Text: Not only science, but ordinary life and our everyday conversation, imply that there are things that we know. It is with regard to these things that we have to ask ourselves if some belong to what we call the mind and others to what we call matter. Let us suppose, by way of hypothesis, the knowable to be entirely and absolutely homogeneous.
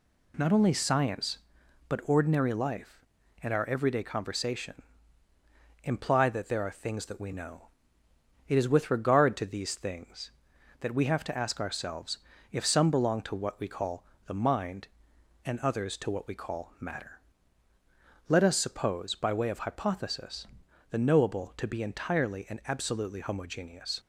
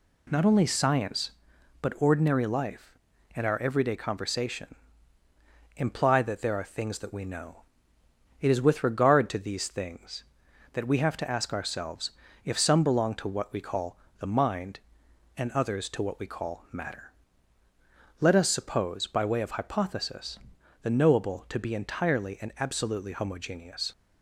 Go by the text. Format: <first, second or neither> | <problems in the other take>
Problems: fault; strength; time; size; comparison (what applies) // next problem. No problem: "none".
neither | pauses between "ourselves" and "if"; slight; the same in both // pauses between "call" and "the"; slight; the same in both